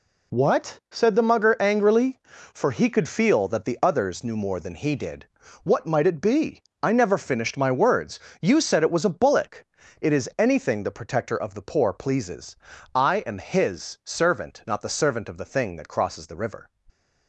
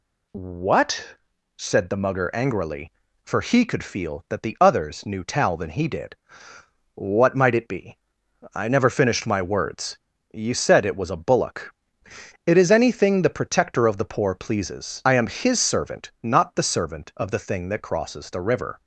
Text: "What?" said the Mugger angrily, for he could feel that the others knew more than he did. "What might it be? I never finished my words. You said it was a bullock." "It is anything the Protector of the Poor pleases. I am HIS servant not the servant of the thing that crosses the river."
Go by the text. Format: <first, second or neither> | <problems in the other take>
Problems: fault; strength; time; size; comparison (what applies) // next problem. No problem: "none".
first | says "tal" for "more"; at 5.2 s